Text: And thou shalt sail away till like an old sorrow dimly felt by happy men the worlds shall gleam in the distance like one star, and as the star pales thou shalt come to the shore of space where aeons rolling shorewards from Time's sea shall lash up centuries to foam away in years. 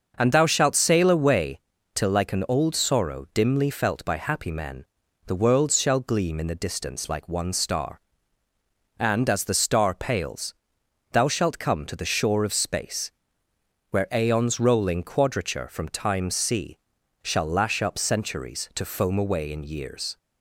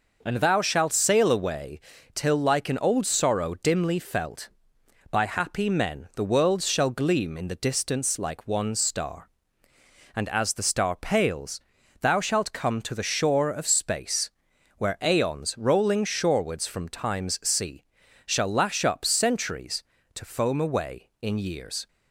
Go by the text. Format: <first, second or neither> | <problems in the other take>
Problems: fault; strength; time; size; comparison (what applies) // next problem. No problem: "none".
second | starts louder than the rest; until 1.1 s; 6 dB // pauses between "away" and "till"; slight; at 1.5 s; 0.34 s long; slight in the second // pauses between "men" and "the"; at 4.8 s; 0.42 s long // pauses between "pales" and "thou"; noticeable; at 10.5 s; 0.58 s long; also in the second // pauses between "space" and "where"; noticeable; at 13.1 s; 0.80 s long; noticeable in the second // says "quadrature" for "shorewards"; at 15.0 s // pauses between "sea" and "shall"; noticeable; at 16.7 s; 0.46 s long; also in the second